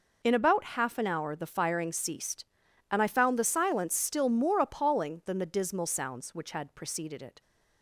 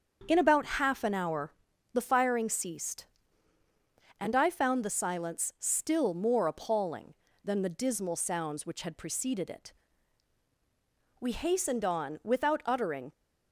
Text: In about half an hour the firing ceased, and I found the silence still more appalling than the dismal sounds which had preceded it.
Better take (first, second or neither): first